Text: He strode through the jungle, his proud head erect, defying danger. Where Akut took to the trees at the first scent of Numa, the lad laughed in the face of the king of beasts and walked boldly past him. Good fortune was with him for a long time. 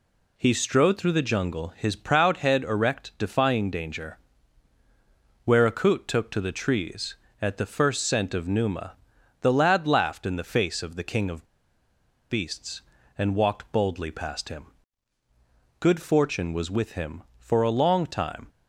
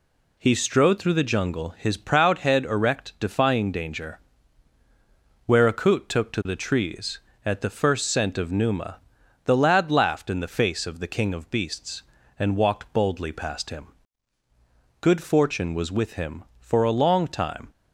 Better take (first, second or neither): second